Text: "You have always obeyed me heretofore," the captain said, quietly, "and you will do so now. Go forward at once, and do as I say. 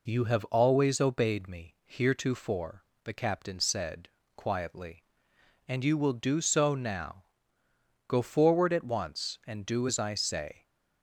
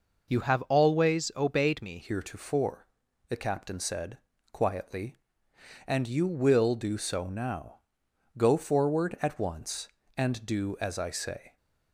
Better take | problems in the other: first | changes voice at "heretofore"; from 2.0 s on; 9.5 s long

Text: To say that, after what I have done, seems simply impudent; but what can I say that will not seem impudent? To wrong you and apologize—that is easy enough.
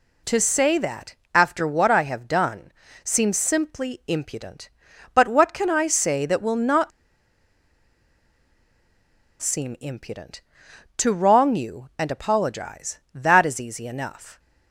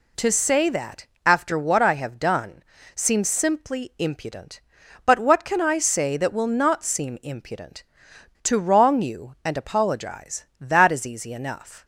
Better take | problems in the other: second | pauses between "not" and "seem"; strong; at 6.9 s; 2.5 s long

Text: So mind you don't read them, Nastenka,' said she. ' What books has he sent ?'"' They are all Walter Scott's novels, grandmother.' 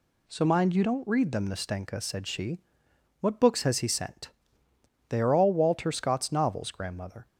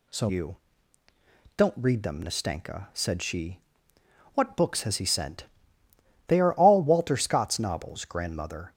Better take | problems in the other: first | skips "mind"; at 0.2 s // pauses between "you" and "don't"; at 0.5 s; 1.0 s long

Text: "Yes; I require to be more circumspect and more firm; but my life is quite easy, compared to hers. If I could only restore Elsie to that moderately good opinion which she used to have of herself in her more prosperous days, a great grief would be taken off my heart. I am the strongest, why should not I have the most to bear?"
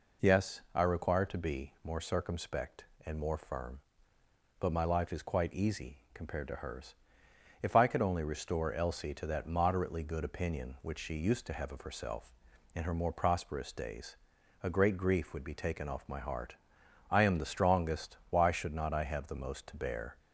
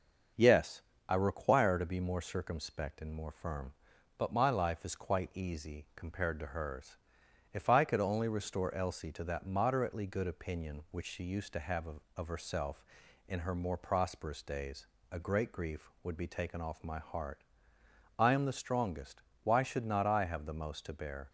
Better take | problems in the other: first | starts louder than the rest; until 1.6 s; 6.5 dB // says "of" twice; at 12.1 s

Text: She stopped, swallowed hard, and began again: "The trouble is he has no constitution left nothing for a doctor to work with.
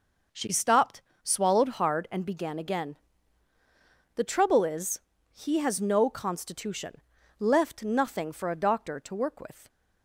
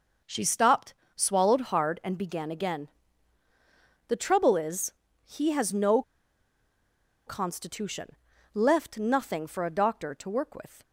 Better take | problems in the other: first | pauses between "is" and "he"; slight; at 4.9 s; 0.32 s long; slight in the first // pauses between "no" and "constitution"; strong; at 6.0 s; 1.2 s long // pauses between "constitution" and "left"; at 8.1 s; 0.40 s long; also in the first

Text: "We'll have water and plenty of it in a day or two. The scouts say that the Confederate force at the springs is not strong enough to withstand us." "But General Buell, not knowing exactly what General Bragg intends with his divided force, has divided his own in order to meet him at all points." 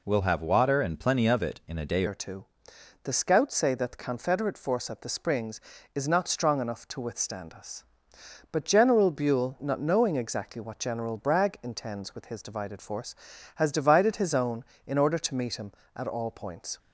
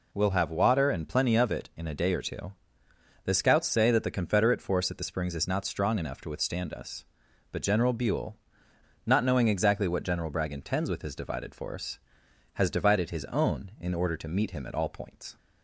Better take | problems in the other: second | changes voice at "or"; from 2.0 s on; 14.7 s long

